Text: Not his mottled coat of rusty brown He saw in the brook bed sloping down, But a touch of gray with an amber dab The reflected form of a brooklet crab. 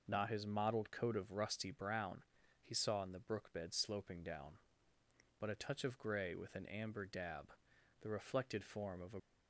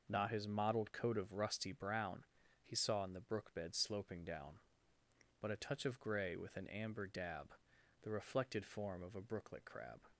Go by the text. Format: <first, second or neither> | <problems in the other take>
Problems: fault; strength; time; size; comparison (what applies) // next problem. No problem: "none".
second | pauses between "brown" and "He"; at 2.2 s; 0.40 s long; also in the second // pauses between "dab" and "The"; noticeable; at 7.5 s; 0.48 s long; noticeable in the second // stops before "brooklet crab"; at 9.1 s